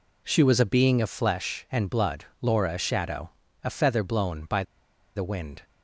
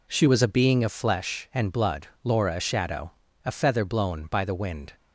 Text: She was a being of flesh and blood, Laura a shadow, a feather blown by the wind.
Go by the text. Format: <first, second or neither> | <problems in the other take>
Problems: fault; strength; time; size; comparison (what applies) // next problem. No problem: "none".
second | pauses between "by" and "the"; noticeable; at 4.6 s; 0.52 s long